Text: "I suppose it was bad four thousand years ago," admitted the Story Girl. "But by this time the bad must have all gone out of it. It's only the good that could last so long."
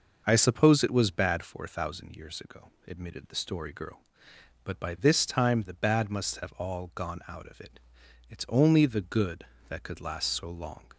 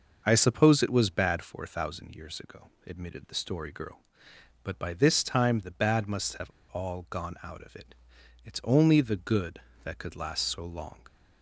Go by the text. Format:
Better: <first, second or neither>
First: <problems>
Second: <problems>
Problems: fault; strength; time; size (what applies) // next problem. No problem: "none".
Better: first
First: none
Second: pauses between "have" and "all"; slight; at 6.4 s; 0.19 s long